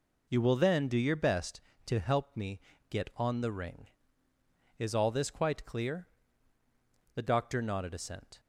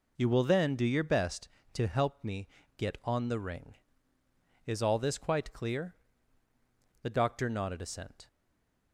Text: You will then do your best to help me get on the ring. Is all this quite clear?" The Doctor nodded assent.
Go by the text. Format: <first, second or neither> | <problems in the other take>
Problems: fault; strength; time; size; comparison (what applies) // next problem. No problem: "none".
first | pauses between "me" and "get"; slight; at 2.4 s; 0.30 s long; slight in the first // stays silent after the last word; slight; from 8.2 s on; 0.7 s long